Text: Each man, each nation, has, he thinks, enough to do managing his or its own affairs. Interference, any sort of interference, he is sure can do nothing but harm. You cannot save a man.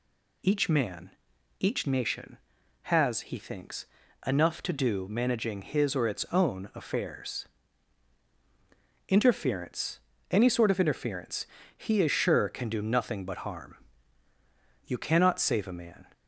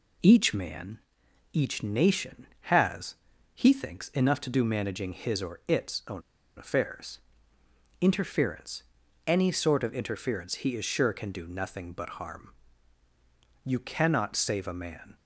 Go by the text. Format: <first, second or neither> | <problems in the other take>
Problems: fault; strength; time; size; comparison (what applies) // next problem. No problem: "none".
first | pauses between "own" and "affairs"; slight; at 6.2 s; 0.35 s long